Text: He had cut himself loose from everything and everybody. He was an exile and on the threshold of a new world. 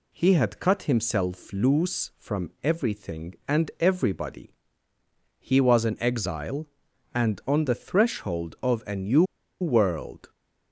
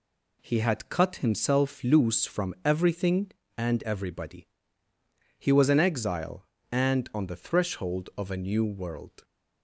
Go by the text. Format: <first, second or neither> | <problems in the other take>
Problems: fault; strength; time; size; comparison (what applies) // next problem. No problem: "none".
second | pauses between "new" and "world"; at 9.2 s; 0.37 s long